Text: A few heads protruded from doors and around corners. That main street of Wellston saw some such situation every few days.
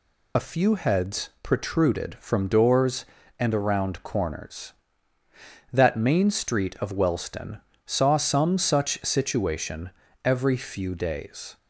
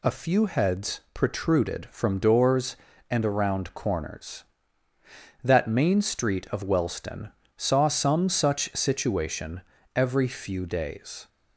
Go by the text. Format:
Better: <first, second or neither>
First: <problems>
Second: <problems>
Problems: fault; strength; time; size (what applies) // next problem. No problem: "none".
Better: second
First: loses the start of "A"; at 0.3 s; 30 ms // pauses between "Wellston" and "saw"; slight; at 7.6 s; 0.24 s long // pauses between "situation" and "every"; slight; at 9.8 s; 0.36 s long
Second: pauses between "Wellston" and "saw"; slight; at 7.3 s; 0.24 s long // pauses between "situation" and "every"; slight; at 9.6 s; 0.36 s long